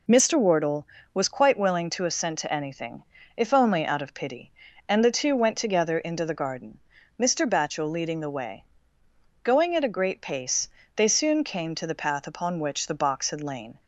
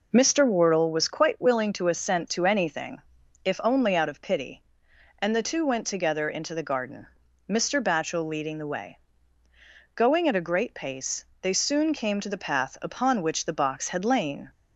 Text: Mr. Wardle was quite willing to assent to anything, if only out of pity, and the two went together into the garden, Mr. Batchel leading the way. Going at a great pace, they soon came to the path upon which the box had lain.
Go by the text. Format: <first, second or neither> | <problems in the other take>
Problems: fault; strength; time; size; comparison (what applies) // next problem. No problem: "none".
neither | none